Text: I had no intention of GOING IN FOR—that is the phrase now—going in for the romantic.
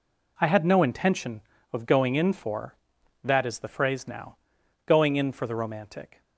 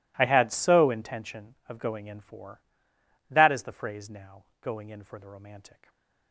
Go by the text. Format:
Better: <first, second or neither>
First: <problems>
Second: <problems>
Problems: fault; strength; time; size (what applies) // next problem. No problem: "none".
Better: first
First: none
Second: says "so" for "no"; at 0.4 s